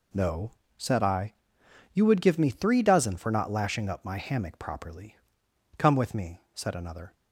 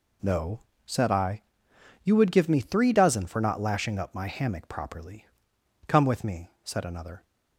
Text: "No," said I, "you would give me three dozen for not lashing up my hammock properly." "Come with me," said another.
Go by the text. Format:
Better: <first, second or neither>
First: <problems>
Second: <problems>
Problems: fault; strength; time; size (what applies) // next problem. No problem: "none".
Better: neither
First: none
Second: none